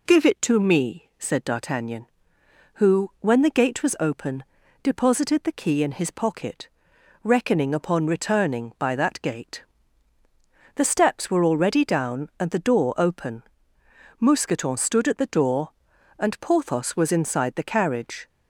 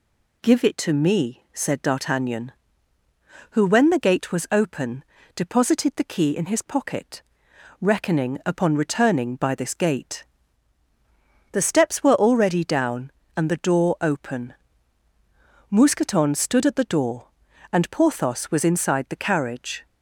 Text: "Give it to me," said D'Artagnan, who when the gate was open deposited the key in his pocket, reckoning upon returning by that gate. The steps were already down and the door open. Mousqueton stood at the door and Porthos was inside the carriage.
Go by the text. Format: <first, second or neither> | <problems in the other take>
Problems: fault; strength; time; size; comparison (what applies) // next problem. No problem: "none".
first | pauses between "open" and "deposited"; slight; at 5.0 s; 0.30 s long; also in the first // says "this" for "that"; at 9.5 s